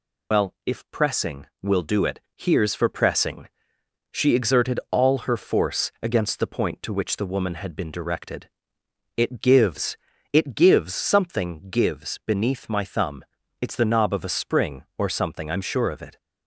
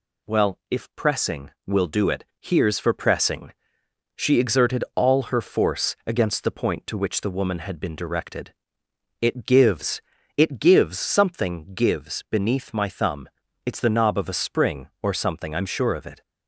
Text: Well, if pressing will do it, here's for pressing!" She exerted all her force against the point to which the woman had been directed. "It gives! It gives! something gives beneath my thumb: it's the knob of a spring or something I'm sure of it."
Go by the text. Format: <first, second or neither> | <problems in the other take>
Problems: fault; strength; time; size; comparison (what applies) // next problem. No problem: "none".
second | loses the start of "Well"; at 0.3 s; 100 ms